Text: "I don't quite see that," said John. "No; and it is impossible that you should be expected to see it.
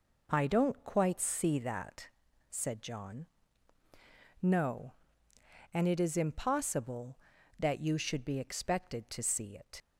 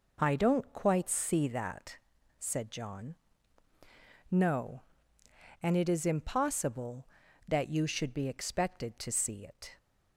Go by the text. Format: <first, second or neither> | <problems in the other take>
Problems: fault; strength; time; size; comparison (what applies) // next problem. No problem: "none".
second | leaves "it" unfinished; at 9.8 s; 80 ms